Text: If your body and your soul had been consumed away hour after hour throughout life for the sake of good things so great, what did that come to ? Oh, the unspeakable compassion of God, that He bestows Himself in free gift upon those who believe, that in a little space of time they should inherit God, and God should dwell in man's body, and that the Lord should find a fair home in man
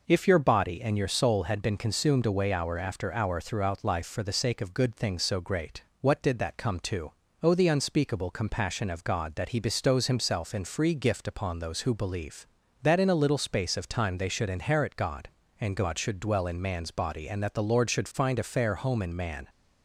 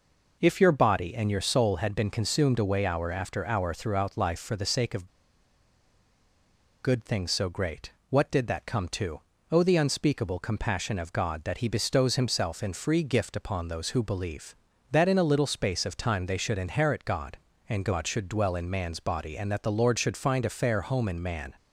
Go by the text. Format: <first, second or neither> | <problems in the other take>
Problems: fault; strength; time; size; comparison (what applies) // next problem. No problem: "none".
first | pauses between "of" and "good"; strong; at 5.0 s; 1.7 s long